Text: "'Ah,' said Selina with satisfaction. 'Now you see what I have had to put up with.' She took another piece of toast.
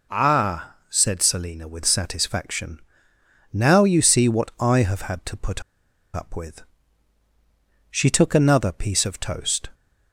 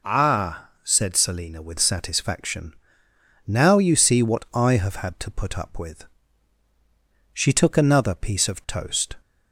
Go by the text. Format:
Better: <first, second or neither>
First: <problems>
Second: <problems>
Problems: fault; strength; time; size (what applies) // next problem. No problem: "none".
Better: second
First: pauses between "put" and "up"; noticeable; at 5.6 s; 0.53 s long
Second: none